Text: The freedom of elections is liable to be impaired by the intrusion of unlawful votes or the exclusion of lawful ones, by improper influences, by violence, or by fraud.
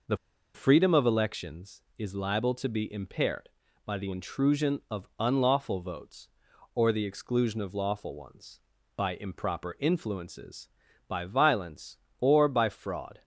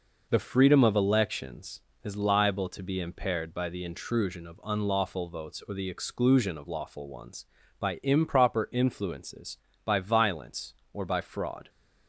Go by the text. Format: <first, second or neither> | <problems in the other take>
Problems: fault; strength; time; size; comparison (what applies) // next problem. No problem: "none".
second | pauses between "The" and "freedom"; at 0.1 s; 0.38 s long